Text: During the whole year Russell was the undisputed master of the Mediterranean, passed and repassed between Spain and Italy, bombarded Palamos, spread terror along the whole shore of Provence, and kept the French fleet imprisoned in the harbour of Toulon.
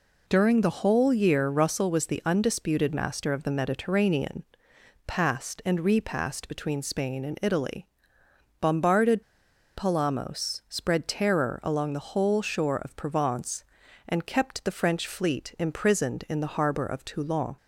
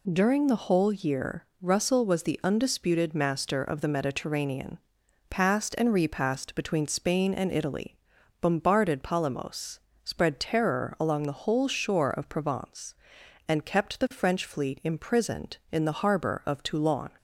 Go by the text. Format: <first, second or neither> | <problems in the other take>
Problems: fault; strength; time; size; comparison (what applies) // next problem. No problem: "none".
second | pauses between "bombarded" and "Palamos"; noticeable; at 9.2 s; 0.53 s long